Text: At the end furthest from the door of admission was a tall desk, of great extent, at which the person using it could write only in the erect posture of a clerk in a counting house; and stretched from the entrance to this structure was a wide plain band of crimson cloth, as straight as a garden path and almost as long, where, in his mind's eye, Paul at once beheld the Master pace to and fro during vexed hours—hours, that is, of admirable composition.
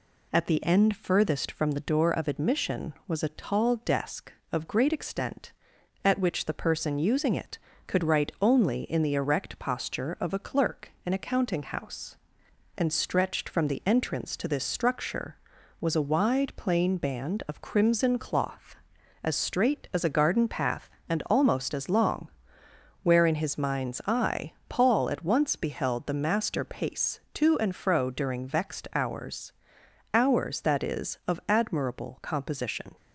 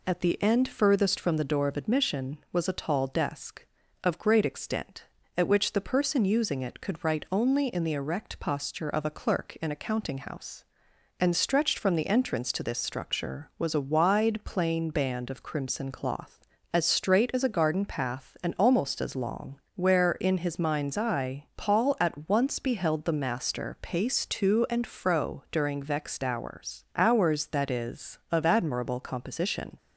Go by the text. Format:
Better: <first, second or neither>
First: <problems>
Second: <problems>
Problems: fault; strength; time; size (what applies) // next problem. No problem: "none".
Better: neither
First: none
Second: none